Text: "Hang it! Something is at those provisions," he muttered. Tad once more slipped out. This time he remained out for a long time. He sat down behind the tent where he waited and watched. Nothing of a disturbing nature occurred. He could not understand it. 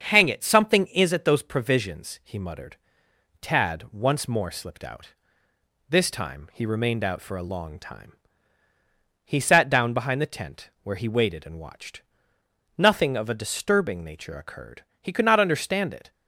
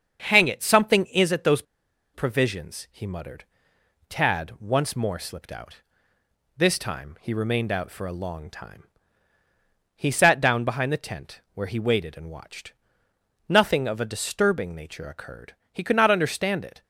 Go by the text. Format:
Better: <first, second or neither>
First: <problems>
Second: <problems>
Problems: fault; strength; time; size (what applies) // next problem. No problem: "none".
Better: first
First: starts louder than the rest; until 1.0 s; 7 dB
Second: starts louder than the rest; until 1.2 s; 7 dB // pauses between "those" and "provisions"; noticeable; at 1.6 s; 0.51 s long